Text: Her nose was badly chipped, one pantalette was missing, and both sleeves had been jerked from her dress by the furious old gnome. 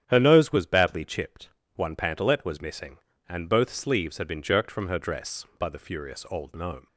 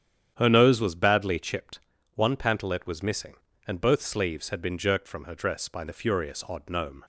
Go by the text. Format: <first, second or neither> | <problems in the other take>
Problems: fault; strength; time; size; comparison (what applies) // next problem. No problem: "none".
first | starts louder than the rest; strong; until 1.3 s; 9 dB; strong in the first // says "odd" for "old"; at 6.4 s